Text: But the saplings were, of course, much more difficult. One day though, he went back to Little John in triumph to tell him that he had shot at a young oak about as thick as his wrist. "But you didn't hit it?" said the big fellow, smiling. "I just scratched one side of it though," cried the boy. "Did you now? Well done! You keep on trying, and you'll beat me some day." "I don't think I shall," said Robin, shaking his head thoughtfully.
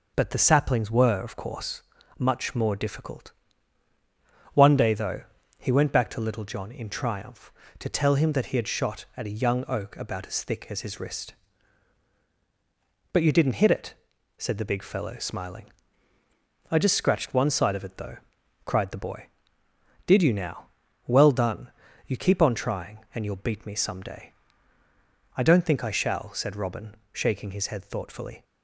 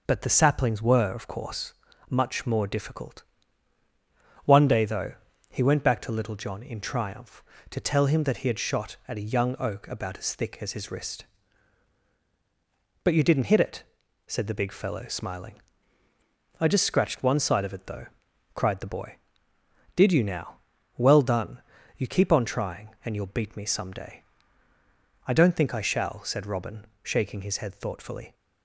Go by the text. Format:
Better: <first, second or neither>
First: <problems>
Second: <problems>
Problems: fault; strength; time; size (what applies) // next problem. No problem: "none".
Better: neither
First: none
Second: none